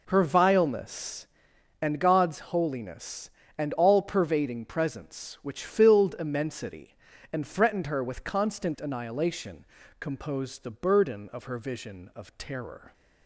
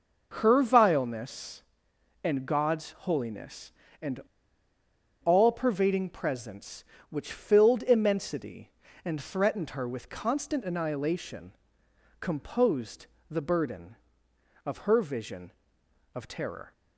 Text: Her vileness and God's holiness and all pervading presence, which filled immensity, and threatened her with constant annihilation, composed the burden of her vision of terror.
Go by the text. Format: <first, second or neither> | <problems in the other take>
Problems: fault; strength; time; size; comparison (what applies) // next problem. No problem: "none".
first | pauses between "and" and "all"; at 4.1 s; 1.0 s long // pauses between "composed" and "the"; slight; at 13.0 s; 0.20 s long